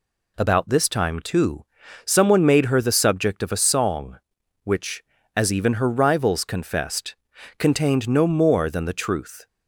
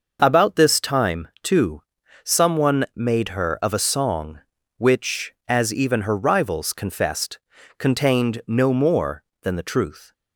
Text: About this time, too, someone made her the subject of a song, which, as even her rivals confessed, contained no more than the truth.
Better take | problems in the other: first | skips "the subject"; at 3.5 s

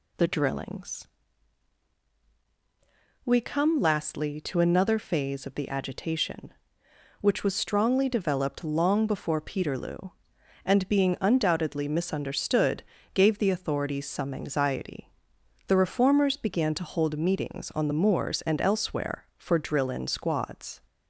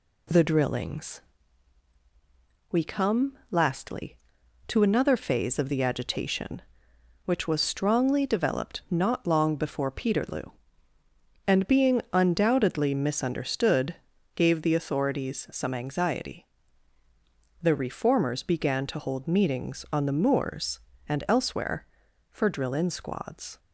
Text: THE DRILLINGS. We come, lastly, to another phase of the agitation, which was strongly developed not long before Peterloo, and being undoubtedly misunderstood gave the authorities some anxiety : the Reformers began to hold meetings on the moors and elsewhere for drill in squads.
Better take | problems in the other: second | skips "not"; at 8.6 s // pauses between "misunderstood" and "gave"; slight; at 12.8 s; 0.30 s long; also in the second

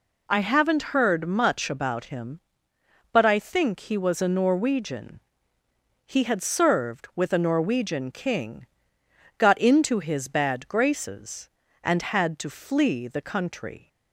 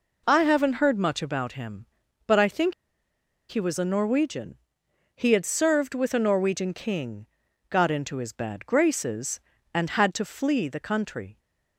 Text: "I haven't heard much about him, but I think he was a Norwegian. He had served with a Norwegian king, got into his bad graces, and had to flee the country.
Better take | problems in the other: first | pauses between "think" and "he"; noticeable; at 2.7 s; 0.77 s long

